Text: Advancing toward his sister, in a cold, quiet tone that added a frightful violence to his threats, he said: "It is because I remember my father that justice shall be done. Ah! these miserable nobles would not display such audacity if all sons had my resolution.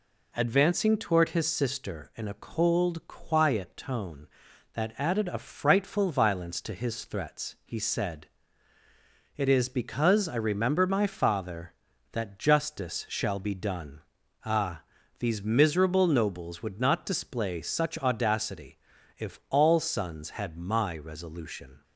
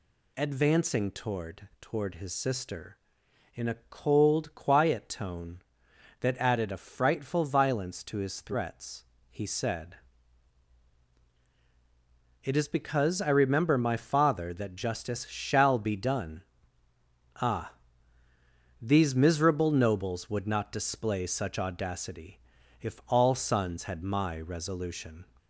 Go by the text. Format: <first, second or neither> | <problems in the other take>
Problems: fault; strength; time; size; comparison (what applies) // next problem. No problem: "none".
first | says "toward" twice; at 1.8 s // pauses between "audacity" and "if"; at 22.3 s; 0.42 s long; also in the first